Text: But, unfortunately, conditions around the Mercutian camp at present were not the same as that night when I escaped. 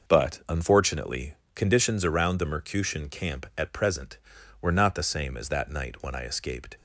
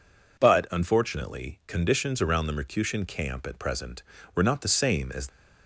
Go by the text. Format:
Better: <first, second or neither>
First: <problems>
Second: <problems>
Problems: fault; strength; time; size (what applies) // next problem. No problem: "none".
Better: first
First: none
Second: stops before "that night when I escaped"; at 5.2 s